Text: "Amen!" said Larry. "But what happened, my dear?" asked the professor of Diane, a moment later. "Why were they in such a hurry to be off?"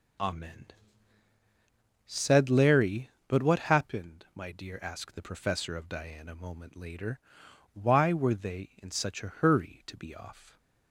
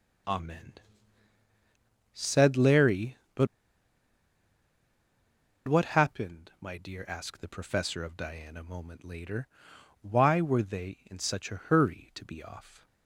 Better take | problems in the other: first | pauses between "But" and "what"; strong; at 3.4 s; 2.2 s long

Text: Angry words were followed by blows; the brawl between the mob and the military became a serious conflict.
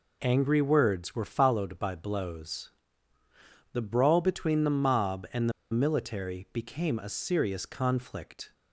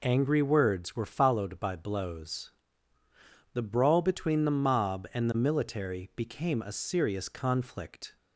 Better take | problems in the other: second | pauses between "the" and "military"; slight; at 5.5 s; 0.20 s long

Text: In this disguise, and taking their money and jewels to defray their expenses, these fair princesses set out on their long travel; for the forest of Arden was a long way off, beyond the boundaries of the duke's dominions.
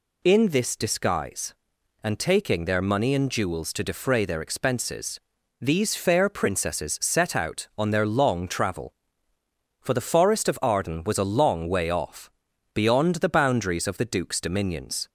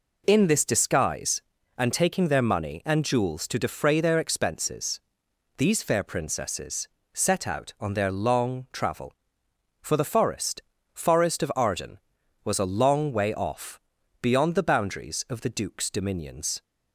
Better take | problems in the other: first | pauses between "princesses" and "set"; slight; at 6.8 s; 0.24 s long // says "forest" twice; at 10.9 s

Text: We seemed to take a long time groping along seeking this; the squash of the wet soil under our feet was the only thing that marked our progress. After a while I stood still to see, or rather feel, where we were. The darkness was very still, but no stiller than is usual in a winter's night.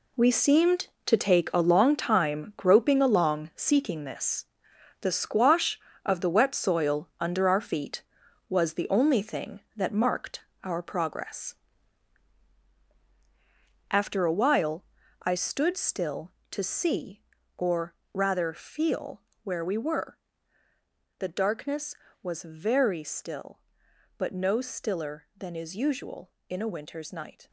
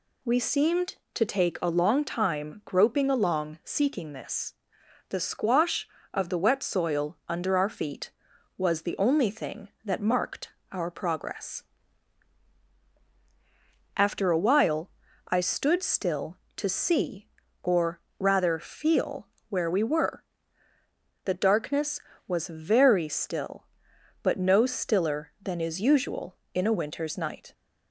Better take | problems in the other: second | gets quieter; strong; throughout; 11 dB // pauses between "marked" and "our"; slight; at 10.4 s; 0.24 s long; slight in the second // pauses between "while" and "I"; at 14.8 s; 0.38 s long; also in the second // pauses between "or" and "rather"; slight; at 17.9 s; 0.16 s long; slight in the second

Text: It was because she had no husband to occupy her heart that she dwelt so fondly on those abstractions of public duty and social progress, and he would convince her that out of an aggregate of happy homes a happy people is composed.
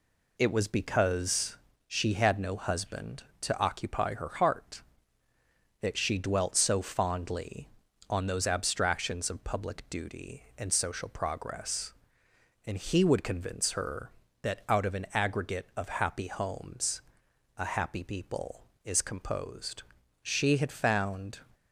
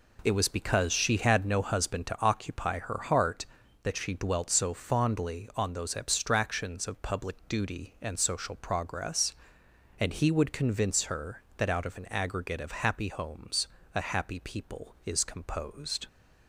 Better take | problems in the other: second | pauses between "because" and "she"; slight; at 1.5 s; 0.30 s long // pauses between "homes" and "a"; noticeable; at 17.0 s; 0.56 s long; slight in the second // goes on to say "She had found"; noticeable; from 20.2 s on; 1.1 s long

